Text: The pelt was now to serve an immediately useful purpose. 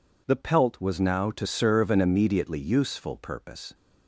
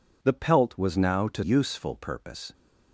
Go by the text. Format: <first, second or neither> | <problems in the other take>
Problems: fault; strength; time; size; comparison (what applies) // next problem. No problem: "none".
first | skips "serve an immediately"; at 1.4 s